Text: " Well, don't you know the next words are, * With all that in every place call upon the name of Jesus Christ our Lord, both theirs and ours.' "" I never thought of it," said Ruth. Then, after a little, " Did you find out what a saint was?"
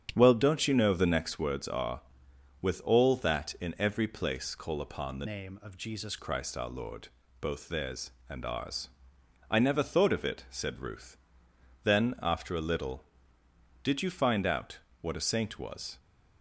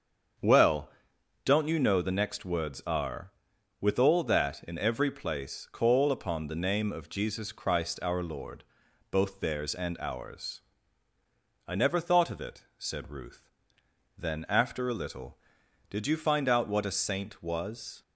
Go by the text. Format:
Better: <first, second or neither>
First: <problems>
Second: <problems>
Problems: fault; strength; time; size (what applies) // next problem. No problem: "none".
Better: second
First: starts louder than the rest; strong; until 1.1 s; 9.5 dB // changes voice from "name" to "Jesus"; from 5.2 to 6.1 s; 0.9 s long // pauses between "out" and "what"; slight; at 14.7 s; 0.22 s long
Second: starts louder than the rest; strong; until 1.9 s; 7 dB